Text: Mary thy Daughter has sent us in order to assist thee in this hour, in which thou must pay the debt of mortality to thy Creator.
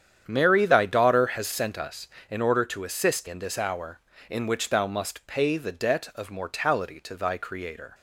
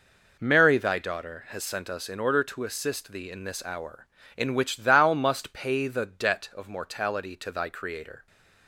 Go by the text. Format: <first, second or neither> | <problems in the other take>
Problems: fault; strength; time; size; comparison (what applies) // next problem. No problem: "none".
second | starts louder than the rest; strong; until 1.2 s; 8.5 dB // skips "thee"; at 3.2 s